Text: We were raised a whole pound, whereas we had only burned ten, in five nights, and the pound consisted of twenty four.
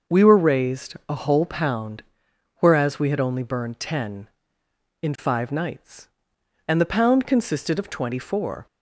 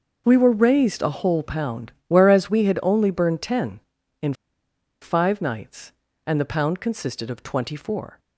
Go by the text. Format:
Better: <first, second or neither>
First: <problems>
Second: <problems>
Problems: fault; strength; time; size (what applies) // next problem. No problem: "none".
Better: first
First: none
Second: pauses between "in" and "five"; noticeable; at 4.3 s; 0.68 s long